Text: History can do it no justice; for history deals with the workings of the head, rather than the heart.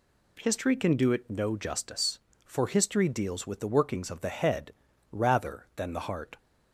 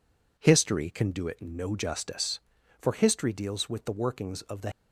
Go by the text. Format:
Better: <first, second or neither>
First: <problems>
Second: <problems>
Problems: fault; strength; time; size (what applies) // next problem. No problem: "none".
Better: first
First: none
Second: stops before "head rather than the heart"; at 4.7 s